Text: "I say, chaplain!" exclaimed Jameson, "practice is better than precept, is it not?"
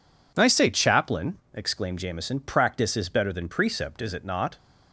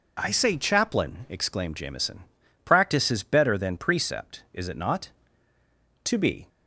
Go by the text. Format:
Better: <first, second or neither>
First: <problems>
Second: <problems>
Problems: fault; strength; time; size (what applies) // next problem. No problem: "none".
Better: first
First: none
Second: goes on to say "To be"; slight; from 6.0 s on; 0.42 s long